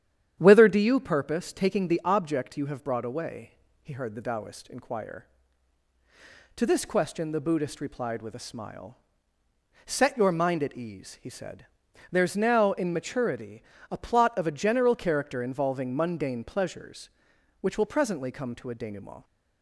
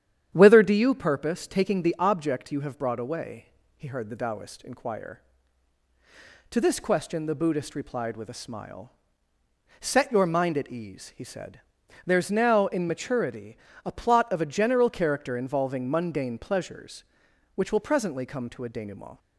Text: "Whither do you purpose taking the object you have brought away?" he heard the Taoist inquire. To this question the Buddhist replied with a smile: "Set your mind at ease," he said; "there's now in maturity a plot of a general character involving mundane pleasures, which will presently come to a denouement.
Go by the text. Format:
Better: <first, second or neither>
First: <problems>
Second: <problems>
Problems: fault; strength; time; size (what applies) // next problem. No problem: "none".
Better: neither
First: starts louder than the rest; strong; until 1.3 s; 9.5 dB // pauses between "maturity" and "a"; slight; at 13.6 s; 0.26 s long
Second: starts louder than the rest; strong; until 1.3 s; 9.5 dB // pauses between "maturity" and "a"; slight; at 13.5 s; 0.26 s long